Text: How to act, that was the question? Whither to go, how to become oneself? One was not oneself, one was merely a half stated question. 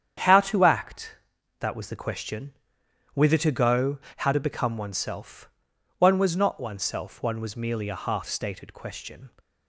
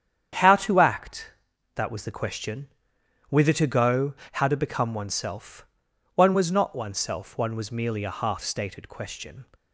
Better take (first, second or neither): neither